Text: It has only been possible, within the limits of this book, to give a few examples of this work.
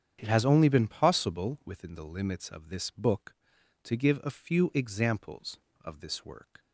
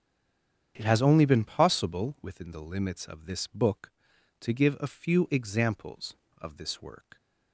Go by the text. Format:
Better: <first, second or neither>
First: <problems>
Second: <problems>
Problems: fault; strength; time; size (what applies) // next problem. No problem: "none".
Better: first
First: starts louder than the rest; strong; until 1.2 s; 8.5 dB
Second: stays silent before the first word; slight; until 0.7 s; 0.7 s long // starts louder than the rest; strong; until 1.7 s; 8.5 dB